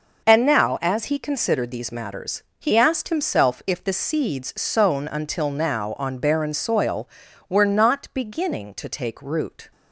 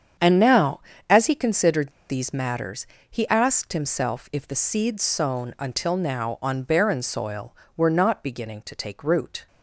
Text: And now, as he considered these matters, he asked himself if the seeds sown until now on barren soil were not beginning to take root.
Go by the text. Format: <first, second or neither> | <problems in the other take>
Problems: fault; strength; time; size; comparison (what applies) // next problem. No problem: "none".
first | starts louder than the rest; strong; until 1.5 s; 8 dB // pauses between "considered" and "these"; slight; at 1.9 s; 0.18 s long